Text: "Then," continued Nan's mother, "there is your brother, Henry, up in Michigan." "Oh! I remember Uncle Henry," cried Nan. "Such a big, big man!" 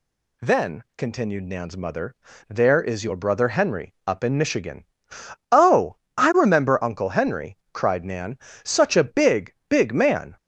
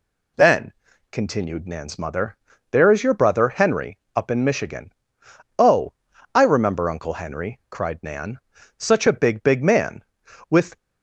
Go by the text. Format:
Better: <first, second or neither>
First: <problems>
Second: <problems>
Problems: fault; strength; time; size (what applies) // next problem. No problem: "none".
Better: first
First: none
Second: goes on to say "With"; slight; from 10.4 s on; 0.26 s long